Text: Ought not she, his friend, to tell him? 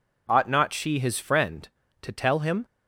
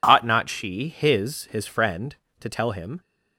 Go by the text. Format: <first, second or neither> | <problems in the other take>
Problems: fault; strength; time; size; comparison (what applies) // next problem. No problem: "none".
first | says "his" twice; at 1.5 s